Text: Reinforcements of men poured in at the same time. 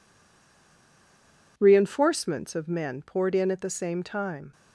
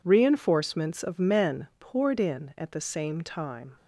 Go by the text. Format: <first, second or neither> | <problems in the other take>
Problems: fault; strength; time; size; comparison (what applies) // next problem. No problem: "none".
second | stays silent before the first word; noticeable; until 1.5 s; 1.5 s long